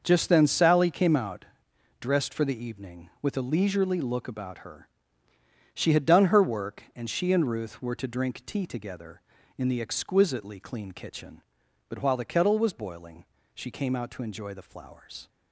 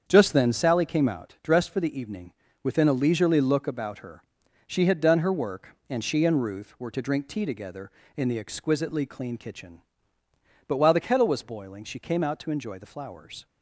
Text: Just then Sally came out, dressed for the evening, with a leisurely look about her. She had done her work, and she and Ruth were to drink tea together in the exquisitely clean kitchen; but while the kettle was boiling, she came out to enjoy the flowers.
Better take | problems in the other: first | starts louder than the rest; strong; until 1.0 s; 7.5 dB; noticeable in the first // says "within" for "with"; at 2.6 s

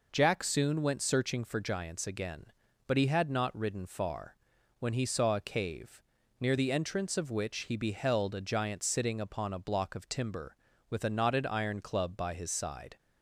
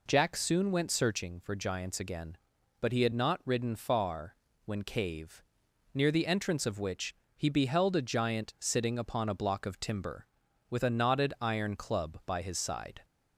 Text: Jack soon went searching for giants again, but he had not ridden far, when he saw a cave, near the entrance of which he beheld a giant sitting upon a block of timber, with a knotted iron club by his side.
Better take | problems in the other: first | skips "he saw a"; at 4.8 s // pauses between "which" and "he"; slight; at 7.1 s; 0.24 s long

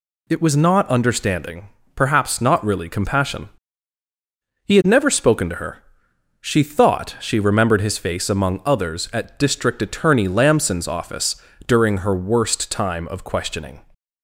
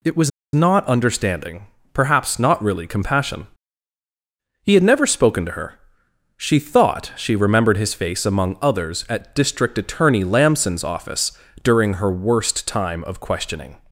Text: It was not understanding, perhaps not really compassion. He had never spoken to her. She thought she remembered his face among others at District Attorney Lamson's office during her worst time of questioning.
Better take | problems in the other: first | pauses between "was" and "not"; slight; at 0.3 s; 0.24 s long // pauses between "office" and "during"; slight; at 11.3 s; 0.32 s long; slight in the first

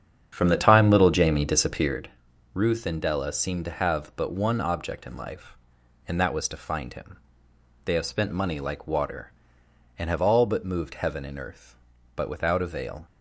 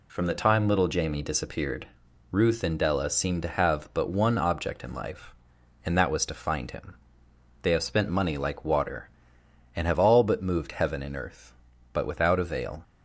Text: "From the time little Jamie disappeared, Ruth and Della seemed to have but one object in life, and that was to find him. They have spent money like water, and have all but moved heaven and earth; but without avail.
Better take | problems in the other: second | starts louder than the rest; strong; until 2.0 s; 8 dB

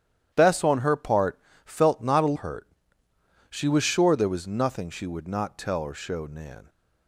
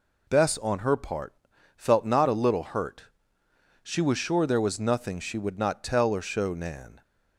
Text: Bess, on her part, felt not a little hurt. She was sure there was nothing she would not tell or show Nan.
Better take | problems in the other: second | starts louder than the rest; strong; until 1.3 s; 10.5 dB // skips "little"; at 2.3 s

